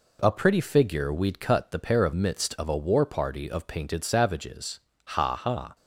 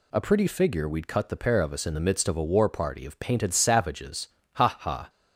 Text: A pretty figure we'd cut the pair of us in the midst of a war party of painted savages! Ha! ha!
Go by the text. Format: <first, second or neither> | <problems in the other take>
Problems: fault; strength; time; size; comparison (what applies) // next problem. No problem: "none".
second | skips "us in the"; at 2.1 s